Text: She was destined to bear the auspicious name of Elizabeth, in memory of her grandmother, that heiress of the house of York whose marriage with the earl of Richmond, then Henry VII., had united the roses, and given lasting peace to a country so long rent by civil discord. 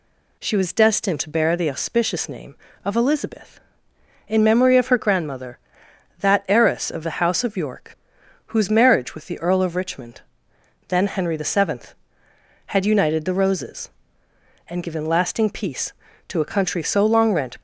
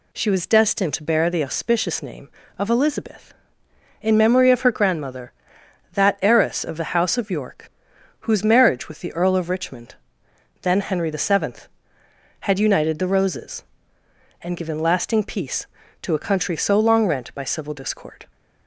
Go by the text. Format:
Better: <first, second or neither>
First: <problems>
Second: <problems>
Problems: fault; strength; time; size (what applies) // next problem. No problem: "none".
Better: second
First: pauses between "York" and "whose"; noticeable; at 7.9 s; 0.54 s long // stops before "by civil discord"; at 17.5 s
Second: pauses between "York" and "whose"; noticeable; at 7.6 s; 0.54 s long